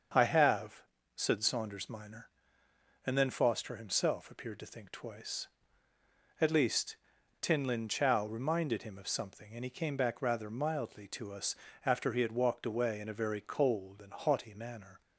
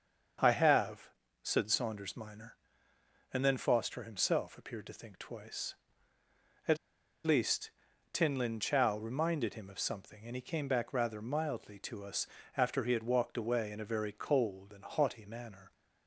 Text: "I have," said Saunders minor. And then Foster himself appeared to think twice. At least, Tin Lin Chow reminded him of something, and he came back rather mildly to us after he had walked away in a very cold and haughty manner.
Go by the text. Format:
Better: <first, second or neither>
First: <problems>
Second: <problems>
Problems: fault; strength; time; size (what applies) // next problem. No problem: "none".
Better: first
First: starts louder than the rest; until 1.4 s; 7 dB // pauses between "us" and "after"; slight; at 11.5 s; 0.30 s long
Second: starts louder than the rest; until 1.7 s; 7 dB // pauses between "At" and "least"; noticeable; at 6.7 s; 0.47 s long // pauses between "us" and "after"; slight; at 12.2 s; 0.30 s long